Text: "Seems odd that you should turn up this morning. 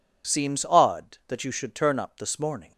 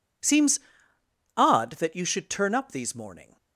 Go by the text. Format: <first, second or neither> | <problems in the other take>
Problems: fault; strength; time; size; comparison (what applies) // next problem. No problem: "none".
first | pauses between "Seems" and "odd"; noticeable; at 0.6 s; 0.74 s long // says "these" for "this"; at 2.7 s